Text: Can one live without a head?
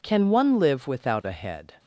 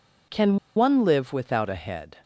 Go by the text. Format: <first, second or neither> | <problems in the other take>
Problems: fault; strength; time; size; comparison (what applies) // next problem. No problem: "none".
first | pauses between "Can" and "one"; slight; at 0.5 s; 0.20 s long